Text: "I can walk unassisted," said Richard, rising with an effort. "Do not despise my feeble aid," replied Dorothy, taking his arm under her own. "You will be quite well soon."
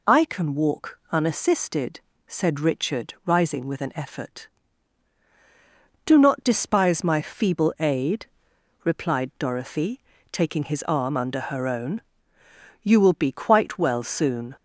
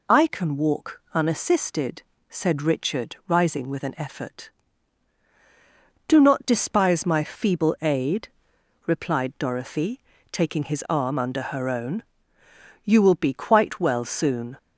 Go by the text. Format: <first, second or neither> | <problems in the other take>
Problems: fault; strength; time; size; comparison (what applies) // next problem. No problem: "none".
neither | none